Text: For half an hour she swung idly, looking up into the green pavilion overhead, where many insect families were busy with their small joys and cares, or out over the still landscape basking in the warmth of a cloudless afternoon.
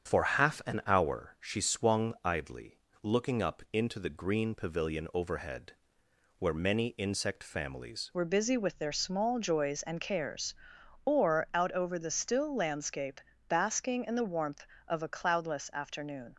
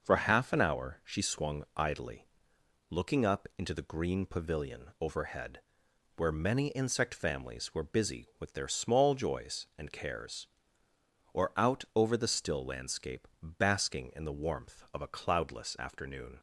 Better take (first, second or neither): second